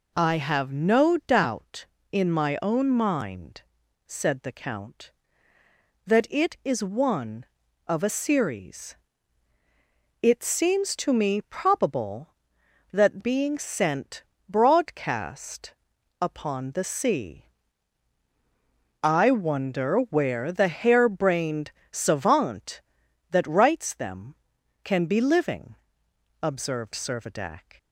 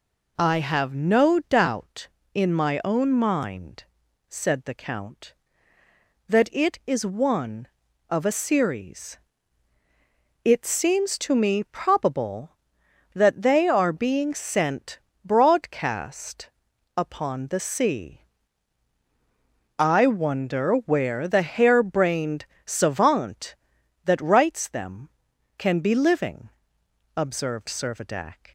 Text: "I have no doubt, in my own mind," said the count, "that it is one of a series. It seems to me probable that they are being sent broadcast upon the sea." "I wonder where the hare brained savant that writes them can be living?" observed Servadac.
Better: second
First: skips "they are"; at 13.2 s // pauses between "sent" and "broadcast"; slight; at 14.2 s; 0.24 s long // pauses between "broadcast" and "upon"; noticeable; at 15.7 s; 0.48 s long // pauses between "brained" and "savant"; slight; at 21.7 s; 0.20 s long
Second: pauses between "sent" and "broadcast"; slight; at 14.9 s; 0.24 s long // pauses between "broadcast" and "upon"; noticeable; at 16.4 s; 0.48 s long // pauses between "brained" and "savant"; slight; at 22.4 s; 0.20 s long

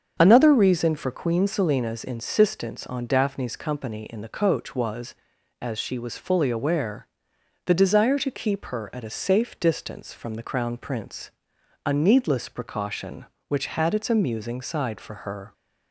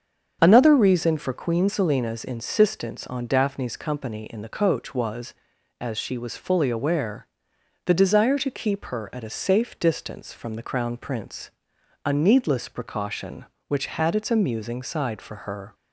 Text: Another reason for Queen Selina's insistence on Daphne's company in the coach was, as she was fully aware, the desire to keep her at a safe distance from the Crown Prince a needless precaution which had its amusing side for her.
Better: neither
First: starts louder than the rest; until 1.1 s; 7 dB // pauses between "Prince" and "a"; noticeable; at 11.3 s; 0.54 s long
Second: starts louder than the rest; until 1.4 s; 7 dB // pauses between "Prince" and "a"; noticeable; at 11.5 s; 0.54 s long

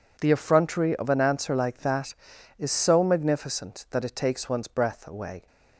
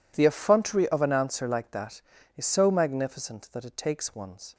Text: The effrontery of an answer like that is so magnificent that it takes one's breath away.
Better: first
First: none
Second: stops before "breath away"; at 4.5 s

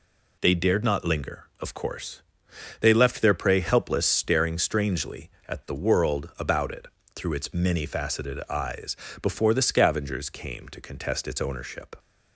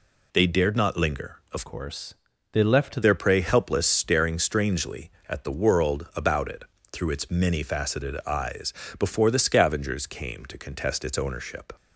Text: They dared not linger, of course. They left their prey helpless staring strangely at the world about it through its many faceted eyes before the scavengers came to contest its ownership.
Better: first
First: pauses between "it" and "through"; slight; at 6.8 s; 0.26 s long // pauses between "eyes" and "before"; slight; at 8.9 s; 0.26 s long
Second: changes voice from "course" to "left"; from 1.6 to 3.0 s; 1.4 s long // pauses between "it" and "through"; slight; at 6.6 s; 0.26 s long // pauses between "eyes" and "before"; slight; at 8.7 s; 0.26 s long

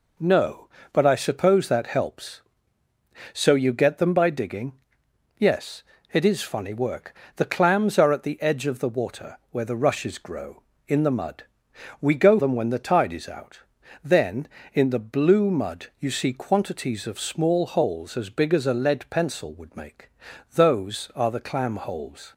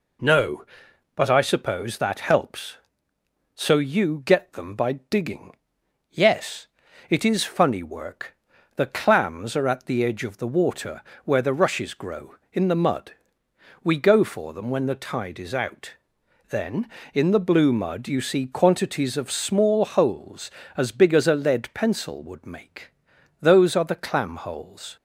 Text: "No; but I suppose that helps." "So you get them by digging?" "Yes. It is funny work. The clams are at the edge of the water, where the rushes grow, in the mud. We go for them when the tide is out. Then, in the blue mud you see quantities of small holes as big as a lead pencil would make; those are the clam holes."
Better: second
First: skips "for"; at 12.3 s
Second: none

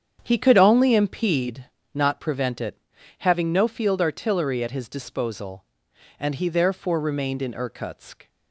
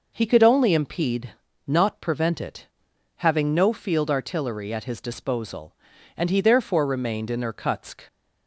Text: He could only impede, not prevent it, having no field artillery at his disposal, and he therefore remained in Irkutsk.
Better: second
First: starts louder than the rest; strong; until 1.6 s; 8 dB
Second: none

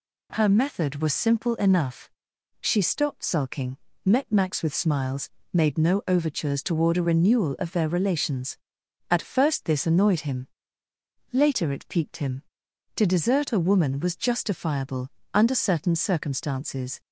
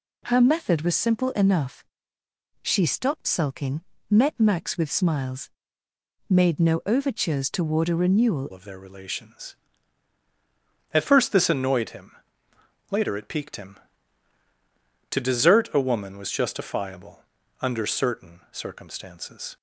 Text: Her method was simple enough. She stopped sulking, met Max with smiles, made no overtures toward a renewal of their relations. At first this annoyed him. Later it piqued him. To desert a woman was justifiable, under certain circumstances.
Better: first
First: none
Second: changes voice at "of"; from 8.5 s on; 11.0 s long

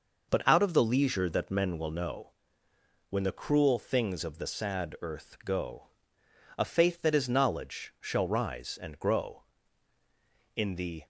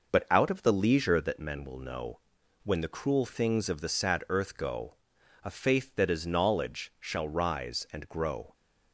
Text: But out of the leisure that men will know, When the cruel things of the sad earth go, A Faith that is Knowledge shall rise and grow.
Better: second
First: goes on to say "In the"; from 10.5 s on; 0.50 s long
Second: none

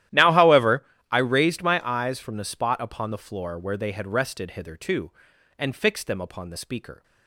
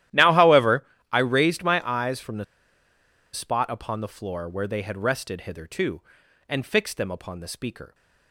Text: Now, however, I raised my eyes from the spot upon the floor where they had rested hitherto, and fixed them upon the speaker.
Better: first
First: starts louder than the rest; strong; until 1.3 s; 13 dB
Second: starts louder than the rest; strong; until 1.3 s; 13 dB // pauses between "the" and "spot"; noticeable; at 2.4 s; 0.89 s long

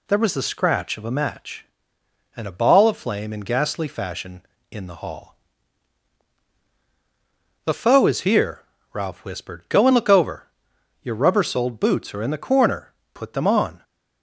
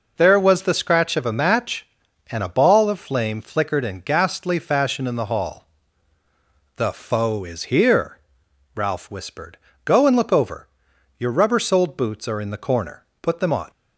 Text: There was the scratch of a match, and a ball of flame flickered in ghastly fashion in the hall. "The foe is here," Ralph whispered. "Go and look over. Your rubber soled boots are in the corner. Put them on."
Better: second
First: skips "flickered"; at 3.3 s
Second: none

